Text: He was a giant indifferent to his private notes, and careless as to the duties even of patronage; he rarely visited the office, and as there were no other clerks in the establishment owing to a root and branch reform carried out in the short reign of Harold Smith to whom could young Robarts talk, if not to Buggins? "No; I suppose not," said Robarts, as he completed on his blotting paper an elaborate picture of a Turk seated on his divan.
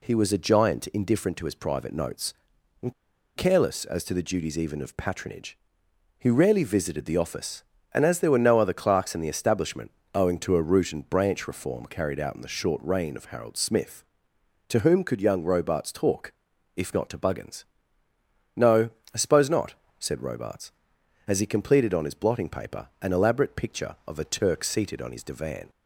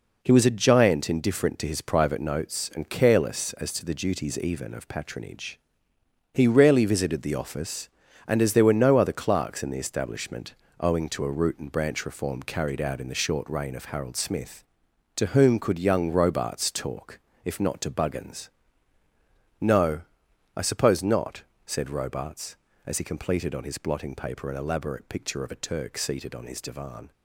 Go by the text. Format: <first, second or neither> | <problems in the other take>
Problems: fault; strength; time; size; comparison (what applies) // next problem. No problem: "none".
second | pauses between "and" and "careless"; at 2.9 s; 0.42 s long // pauses between "establishment" and "owing"; slight; at 9.8 s; 0.24 s long; slight in the second // pauses between "paper" and "an"; slight; at 22.8 s; 0.16 s long